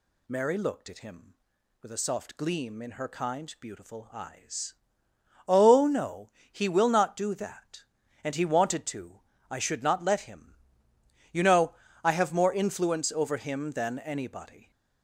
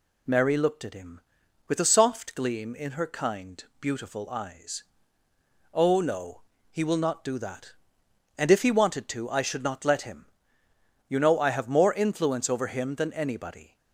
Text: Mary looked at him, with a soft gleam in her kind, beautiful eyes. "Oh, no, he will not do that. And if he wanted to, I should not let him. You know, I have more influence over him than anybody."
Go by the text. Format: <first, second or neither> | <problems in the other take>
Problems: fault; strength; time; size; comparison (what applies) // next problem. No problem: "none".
second | skips "if"; at 8.3 s